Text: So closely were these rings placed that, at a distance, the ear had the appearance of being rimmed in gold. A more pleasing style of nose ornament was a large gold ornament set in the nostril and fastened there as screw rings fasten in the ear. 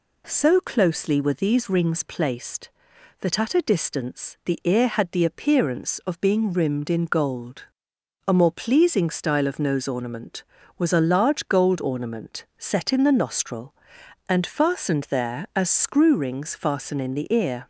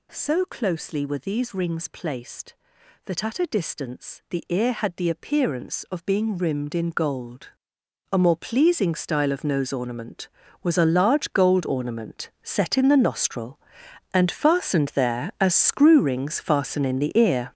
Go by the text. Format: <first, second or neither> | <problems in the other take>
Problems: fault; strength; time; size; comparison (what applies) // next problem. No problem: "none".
first | gets louder; strong; throughout; 10.5 dB